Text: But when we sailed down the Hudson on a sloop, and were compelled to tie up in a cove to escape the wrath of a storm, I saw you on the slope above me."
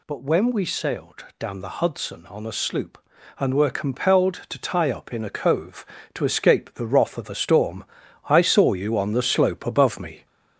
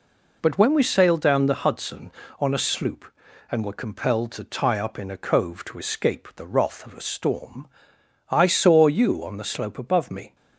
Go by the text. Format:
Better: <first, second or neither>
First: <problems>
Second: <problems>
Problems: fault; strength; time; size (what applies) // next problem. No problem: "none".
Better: second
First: gets louder; slight; throughout; 3.5 dB // pauses between "sailed" and "down"; slight; at 1.2 s; 0.16 s long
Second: none